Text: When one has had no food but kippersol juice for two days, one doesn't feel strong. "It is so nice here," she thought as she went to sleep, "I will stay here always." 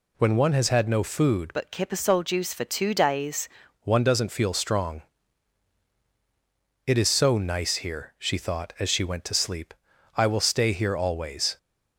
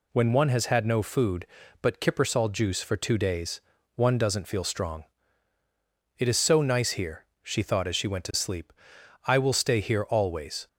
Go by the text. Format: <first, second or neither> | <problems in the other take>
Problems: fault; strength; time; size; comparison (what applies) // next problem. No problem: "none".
second | changes voice from "but" to "days"; from 1.5 to 3.4 s; 1.9 s long